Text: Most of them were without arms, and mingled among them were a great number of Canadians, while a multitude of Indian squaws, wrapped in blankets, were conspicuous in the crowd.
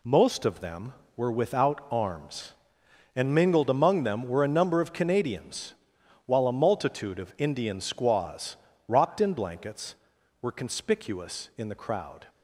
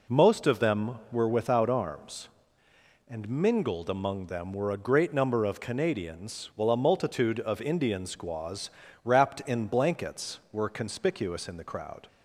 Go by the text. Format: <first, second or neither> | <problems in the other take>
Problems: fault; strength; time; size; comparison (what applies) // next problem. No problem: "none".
second | skips "great"; at 4.4 s